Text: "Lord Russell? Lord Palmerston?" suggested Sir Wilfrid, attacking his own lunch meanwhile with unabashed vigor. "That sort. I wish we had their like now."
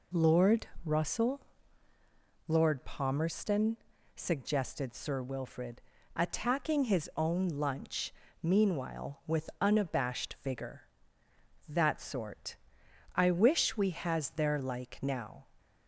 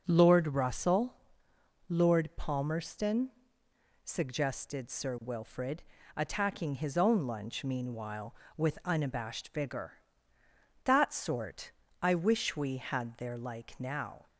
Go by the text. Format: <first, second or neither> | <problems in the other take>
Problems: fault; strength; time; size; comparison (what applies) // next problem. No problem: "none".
second | pauses between "Lord" and "Russell"; slight; at 0.6 s; 0.18 s long // pauses between "lunch" and "meanwhile"; slight; at 8.1 s; 0.30 s long // says "has" for "had"; at 13.9 s